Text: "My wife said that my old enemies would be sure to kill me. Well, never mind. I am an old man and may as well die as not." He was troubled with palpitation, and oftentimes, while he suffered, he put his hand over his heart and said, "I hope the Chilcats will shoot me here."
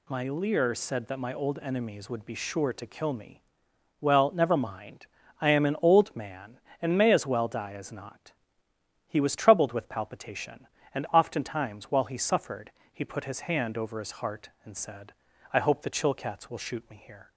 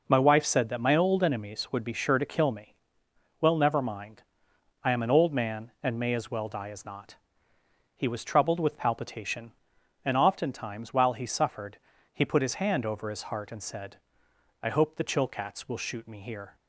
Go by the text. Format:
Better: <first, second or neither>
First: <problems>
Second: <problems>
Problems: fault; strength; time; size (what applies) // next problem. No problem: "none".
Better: second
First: says "leer" for "wife"; at 0.2 s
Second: none